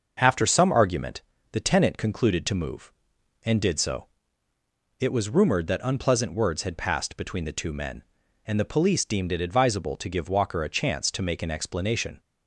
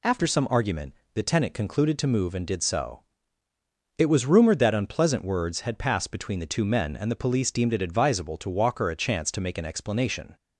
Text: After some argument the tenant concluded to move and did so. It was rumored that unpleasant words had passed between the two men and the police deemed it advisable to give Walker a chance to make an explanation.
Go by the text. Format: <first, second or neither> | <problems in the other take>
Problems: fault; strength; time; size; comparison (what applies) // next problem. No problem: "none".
first | pauses between "argument" and "the"; slight; at 0.9 s; 0.22 s long; slight in the first // skips "give"; at 8.4 s